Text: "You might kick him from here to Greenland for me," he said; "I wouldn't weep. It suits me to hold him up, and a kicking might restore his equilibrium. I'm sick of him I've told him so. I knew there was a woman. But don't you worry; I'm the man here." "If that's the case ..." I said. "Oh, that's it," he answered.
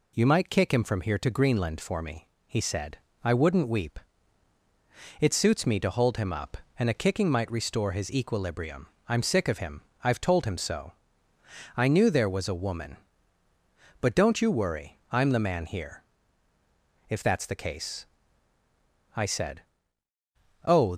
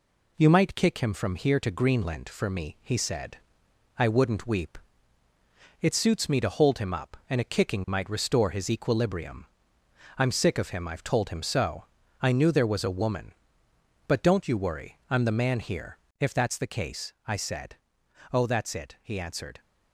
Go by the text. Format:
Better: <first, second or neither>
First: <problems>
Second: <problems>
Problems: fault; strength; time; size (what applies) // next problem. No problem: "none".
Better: second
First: pauses between "him" and "I've"; slight; at 9.8 s; 0.22 s long // stops before "that's it he answered"; at 20.9 s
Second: none